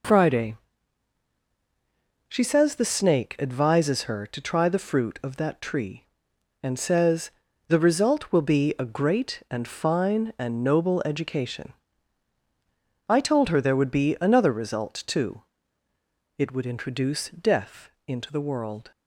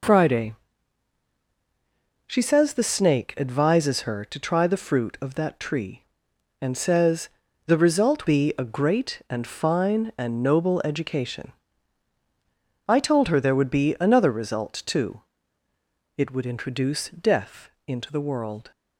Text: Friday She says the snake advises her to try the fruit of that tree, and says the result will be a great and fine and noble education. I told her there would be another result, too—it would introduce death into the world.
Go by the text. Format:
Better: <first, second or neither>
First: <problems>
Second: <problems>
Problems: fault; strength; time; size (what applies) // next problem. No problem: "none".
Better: first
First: pauses between "Friday" and "She"; strong; at 0.5 s; 1.7 s long // pauses between "says" and "the"; at 7.3 s; 0.38 s long // pauses between "death" and "into"; slight; at 17.8 s; 0.18 s long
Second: pauses between "Friday" and "She"; strong; at 0.5 s; 1.7 s long // pauses between "says" and "the"; at 7.2 s; 0.38 s long // skips "will"; at 8.2 s // pauses between "death" and "into"; slight; at 17.6 s; 0.18 s long